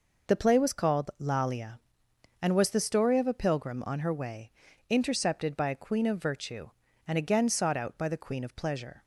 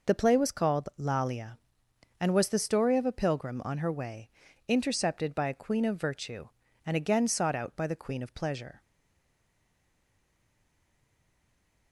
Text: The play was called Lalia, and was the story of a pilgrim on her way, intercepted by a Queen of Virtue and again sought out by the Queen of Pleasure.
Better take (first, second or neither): first